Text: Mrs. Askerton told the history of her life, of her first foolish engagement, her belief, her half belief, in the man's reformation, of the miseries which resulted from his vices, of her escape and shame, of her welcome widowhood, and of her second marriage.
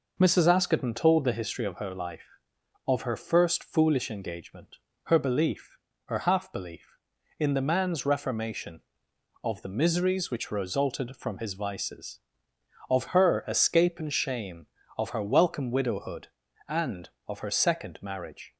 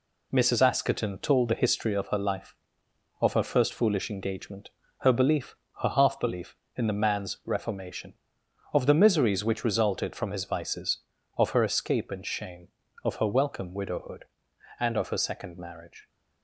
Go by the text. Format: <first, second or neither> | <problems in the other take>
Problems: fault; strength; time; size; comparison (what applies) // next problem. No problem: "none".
first | gets quieter; noticeable; throughout; 5.5 dB